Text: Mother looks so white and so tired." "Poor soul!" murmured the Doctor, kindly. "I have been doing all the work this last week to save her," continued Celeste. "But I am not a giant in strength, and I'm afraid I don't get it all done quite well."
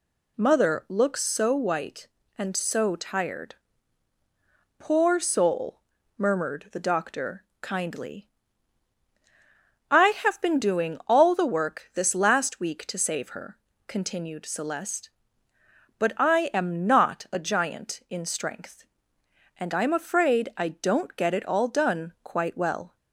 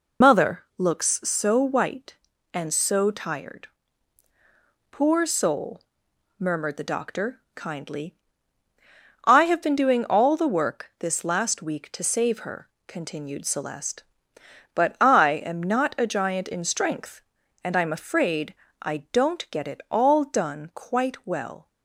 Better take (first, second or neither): first